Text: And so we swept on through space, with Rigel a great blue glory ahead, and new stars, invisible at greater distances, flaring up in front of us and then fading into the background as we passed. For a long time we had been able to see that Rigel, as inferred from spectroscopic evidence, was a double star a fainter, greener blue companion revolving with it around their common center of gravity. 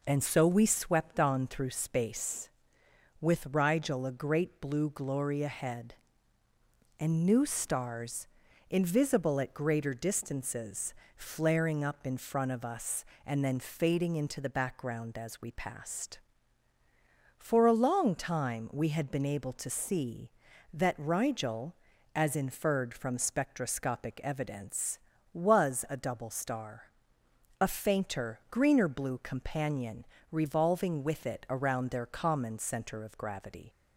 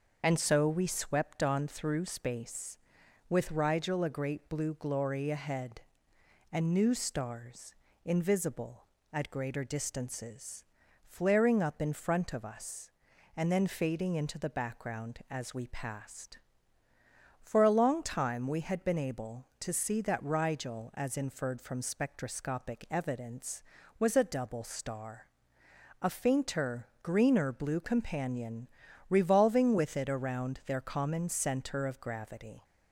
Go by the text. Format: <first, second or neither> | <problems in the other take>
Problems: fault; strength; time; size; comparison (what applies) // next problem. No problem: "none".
first | loses the start of "And"; at 0.2 s; 30 ms // starts louder than the rest; until 1.2 s; 6 dB // pauses between "star" and "a"; noticeable; at 25.2 s; 0.76 s long; noticeable in the first // pauses between "companion" and "revolving"; at 28.6 s; 0.42 s long; slight in the first